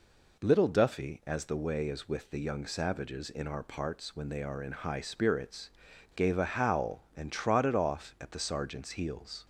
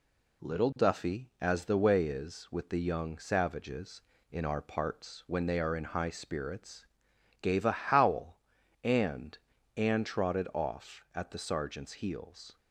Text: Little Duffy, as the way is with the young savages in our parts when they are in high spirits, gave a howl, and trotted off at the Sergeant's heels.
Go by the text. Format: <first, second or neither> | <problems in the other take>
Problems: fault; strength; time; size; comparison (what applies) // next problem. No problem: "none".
first | says "and" twice; at 9.7 s